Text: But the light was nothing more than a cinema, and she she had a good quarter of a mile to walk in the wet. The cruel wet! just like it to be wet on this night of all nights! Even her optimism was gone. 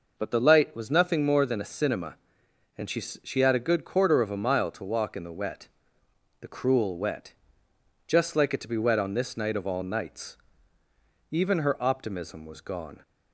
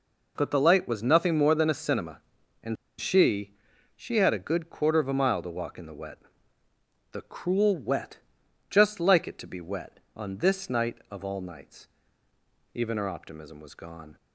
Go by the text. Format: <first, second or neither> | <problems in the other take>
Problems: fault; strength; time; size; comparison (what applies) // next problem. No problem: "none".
first | pauses between "and" and "she"; slight; at 2.7 s; 0.24 s long // pauses between "she" and "she"; at 3.5 s; 0.42 s long